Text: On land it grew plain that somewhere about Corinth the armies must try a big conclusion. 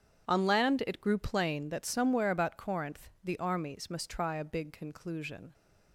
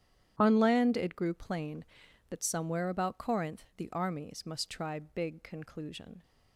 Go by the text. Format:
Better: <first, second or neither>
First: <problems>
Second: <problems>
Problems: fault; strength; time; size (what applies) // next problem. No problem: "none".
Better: first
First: starts louder than the rest; strong; until 1.3 s; 8 dB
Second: starts louder than the rest; strong; until 1.3 s; 10.5 dB // skips "a"; at 4.9 s